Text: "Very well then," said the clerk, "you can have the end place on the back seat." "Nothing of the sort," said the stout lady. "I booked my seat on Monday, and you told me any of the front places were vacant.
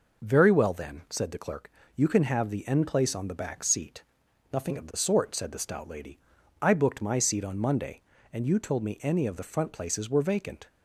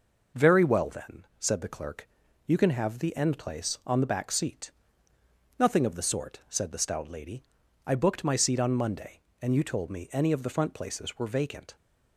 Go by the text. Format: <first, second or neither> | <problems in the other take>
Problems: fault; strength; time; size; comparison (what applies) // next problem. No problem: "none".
neither | none